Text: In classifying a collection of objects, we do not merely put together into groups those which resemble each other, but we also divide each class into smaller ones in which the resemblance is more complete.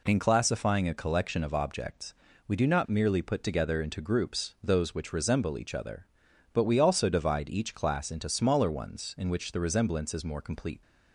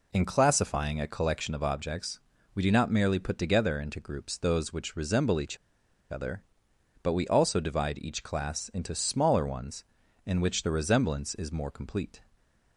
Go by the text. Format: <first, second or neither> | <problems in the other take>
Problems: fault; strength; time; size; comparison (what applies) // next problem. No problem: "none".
first | pauses between "each" and "other"; noticeable; at 5.5 s; 0.53 s long